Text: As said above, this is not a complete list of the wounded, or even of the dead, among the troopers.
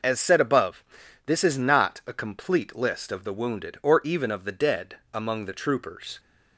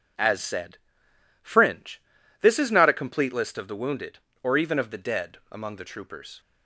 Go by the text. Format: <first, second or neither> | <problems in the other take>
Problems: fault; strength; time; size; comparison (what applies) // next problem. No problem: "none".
first | says "fringe" for "above"; at 1.4 s